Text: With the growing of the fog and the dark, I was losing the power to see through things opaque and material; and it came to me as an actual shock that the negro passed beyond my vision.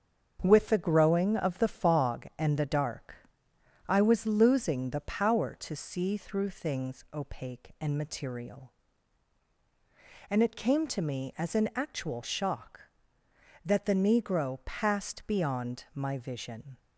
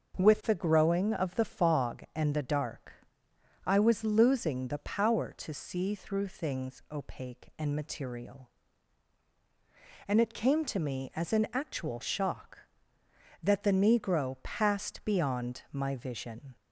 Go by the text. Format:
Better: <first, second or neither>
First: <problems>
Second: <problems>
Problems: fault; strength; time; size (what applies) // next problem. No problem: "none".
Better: second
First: gets quieter; throughout; 6 dB // starts louder than the rest; until 1.4 s; 7 dB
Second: starts louder than the rest; until 1.2 s; 6.5 dB